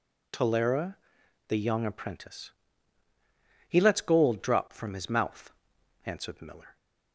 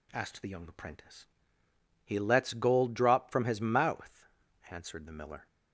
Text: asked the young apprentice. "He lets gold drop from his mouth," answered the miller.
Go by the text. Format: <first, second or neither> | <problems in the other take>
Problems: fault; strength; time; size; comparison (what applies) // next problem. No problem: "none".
second | says "tolera" for "asked"; at 0.3 s